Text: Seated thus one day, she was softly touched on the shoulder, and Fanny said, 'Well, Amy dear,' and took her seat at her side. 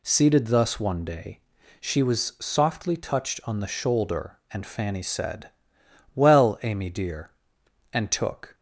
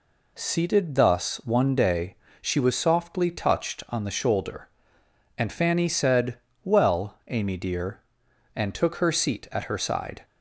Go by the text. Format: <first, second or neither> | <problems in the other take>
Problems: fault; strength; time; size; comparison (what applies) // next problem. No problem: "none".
second | stops before "her seat at her side"; at 8.5 s